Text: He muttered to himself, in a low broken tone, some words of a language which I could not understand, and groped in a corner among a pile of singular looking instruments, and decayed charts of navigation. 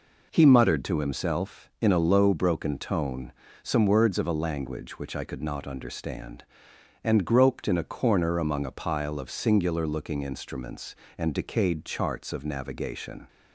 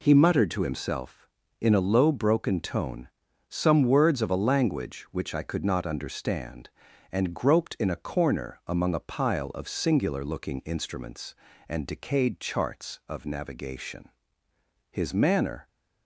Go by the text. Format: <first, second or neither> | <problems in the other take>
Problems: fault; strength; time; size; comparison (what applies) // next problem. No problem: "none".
first | goes on to say "His manner"; noticeable; from 14.8 s on; 0.78 s long